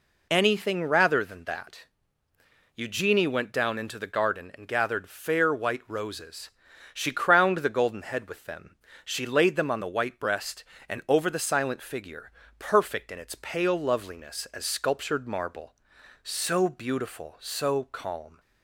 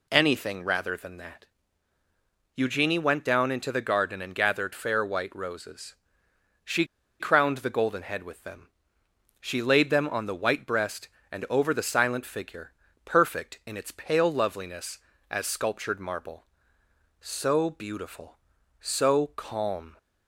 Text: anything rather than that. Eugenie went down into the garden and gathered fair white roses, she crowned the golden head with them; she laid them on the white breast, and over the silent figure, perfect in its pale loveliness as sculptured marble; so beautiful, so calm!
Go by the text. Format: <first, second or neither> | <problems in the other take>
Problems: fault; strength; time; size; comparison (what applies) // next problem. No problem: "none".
first | pauses between "she" and "crowned"; slight; at 6.8 s; 0.35 s long